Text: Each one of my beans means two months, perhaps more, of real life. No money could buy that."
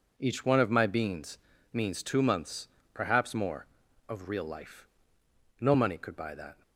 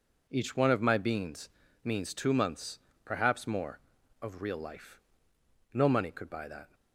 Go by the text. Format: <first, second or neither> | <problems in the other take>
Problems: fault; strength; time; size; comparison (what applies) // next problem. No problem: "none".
neither | pauses between "beans" and "means"; slight; the same in both